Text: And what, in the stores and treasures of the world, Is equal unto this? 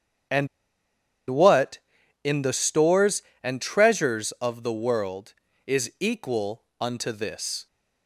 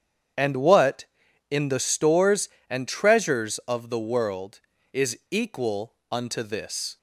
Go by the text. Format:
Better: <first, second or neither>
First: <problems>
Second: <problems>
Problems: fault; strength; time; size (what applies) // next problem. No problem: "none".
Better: second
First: starts louder than the rest; strong; until 2.5 s; 8.5 dB // pauses between "And" and "what"; noticeable; at 0.4 s; 0.83 s long // pauses between "equal" and "unto"; slight; at 6.6 s; 0.16 s long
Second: starts louder than the rest; strong; until 1.8 s; 8.5 dB // pauses between "equal" and "unto"; slight; at 5.9 s; 0.16 s long